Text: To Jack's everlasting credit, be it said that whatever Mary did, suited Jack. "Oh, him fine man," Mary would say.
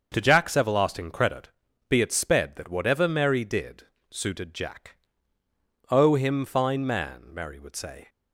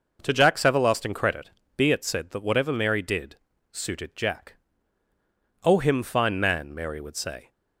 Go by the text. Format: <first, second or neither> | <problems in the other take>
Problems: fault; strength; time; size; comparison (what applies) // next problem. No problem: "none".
second | starts louder than the rest; until 1.1 s; 6.5 dB // says "sped" for "said"; at 2.1 s